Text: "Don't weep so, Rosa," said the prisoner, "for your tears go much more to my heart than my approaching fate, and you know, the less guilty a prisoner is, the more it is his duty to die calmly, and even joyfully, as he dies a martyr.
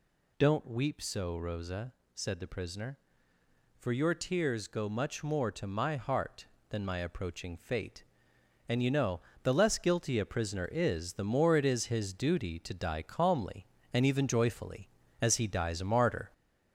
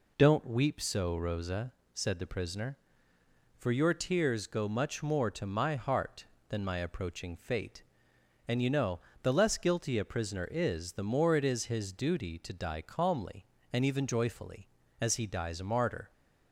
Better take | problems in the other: second | gets louder; noticeable; throughout; 4.5 dB

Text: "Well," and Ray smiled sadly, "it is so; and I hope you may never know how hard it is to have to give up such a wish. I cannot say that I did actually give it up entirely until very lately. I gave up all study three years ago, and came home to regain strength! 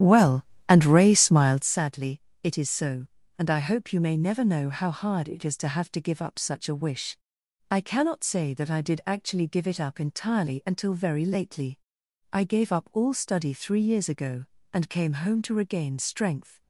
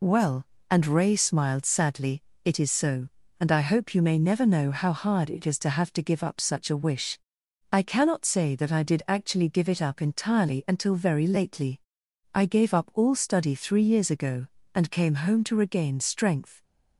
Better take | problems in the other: second | starts louder than the rest; strong; until 1.7 s; 11 dB

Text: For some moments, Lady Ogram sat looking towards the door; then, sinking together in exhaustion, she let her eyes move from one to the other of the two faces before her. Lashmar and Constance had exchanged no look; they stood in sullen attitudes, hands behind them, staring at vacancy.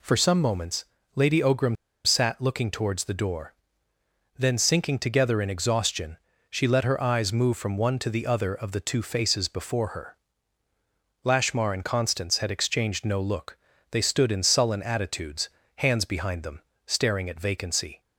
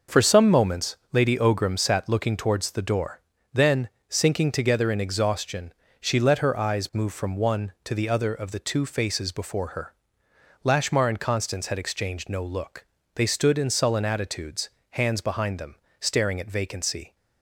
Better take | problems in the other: second | pauses between "Ogram" and "sat"; slight; at 1.7 s; 0.30 s long

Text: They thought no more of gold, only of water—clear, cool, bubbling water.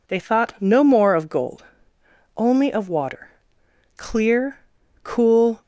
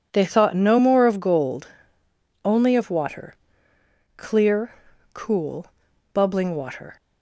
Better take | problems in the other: second | stops before "bubbling water"; at 5.6 s

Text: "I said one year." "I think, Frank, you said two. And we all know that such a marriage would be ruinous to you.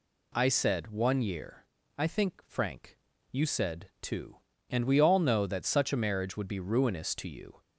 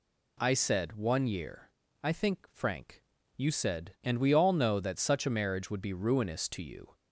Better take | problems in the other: first | skips "two"; at 3.9 s

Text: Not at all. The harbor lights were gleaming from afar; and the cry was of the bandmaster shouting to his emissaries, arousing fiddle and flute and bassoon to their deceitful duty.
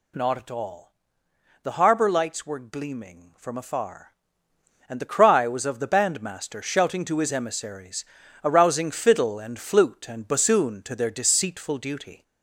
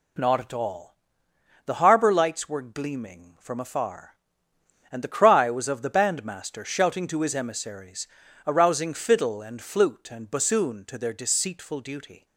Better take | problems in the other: second | gets louder; slight; throughout; 3 dB

